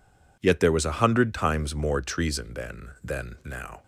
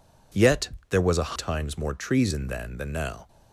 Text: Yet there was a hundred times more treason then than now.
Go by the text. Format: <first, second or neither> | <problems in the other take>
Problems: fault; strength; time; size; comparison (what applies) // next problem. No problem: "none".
first | pauses between "Yet" and "there"; slight; at 0.6 s; 0.20 s long // skips "hundred"; at 1.3 s